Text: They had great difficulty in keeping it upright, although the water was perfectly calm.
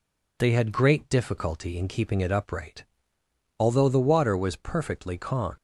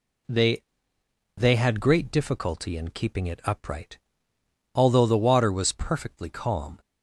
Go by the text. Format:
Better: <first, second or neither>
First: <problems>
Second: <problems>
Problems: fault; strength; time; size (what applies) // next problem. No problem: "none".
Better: first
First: none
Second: says "They" twice; at 1.3 s